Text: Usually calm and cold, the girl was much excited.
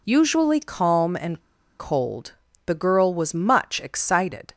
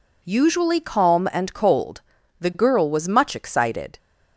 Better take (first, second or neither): second